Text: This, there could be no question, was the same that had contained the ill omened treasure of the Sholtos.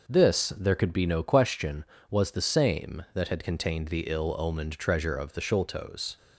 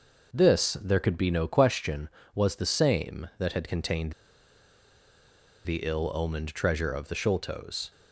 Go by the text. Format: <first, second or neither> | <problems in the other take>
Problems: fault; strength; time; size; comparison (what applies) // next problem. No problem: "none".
first | pauses between "contained" and "the"; strong; at 4.1 s; 1.5 s long